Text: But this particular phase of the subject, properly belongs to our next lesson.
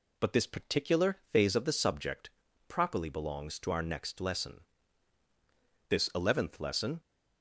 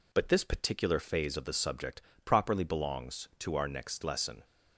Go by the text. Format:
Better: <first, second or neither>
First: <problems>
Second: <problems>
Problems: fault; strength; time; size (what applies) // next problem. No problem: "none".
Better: second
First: goes on to say "This Eleventh Lesson"; noticeable; from 5.8 s on; 1.1 s long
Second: none